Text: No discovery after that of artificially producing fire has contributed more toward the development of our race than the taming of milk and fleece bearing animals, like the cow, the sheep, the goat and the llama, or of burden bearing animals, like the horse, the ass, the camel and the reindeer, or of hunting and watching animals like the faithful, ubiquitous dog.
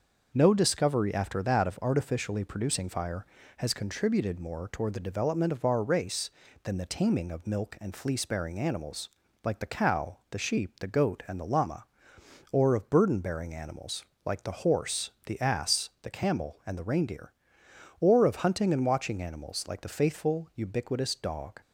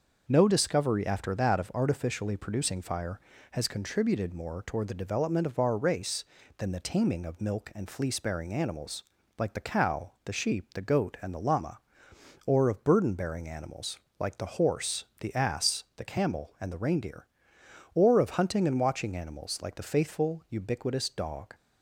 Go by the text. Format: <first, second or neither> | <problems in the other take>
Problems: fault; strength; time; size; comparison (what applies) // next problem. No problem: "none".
neither | starts louder than the rest; the same in both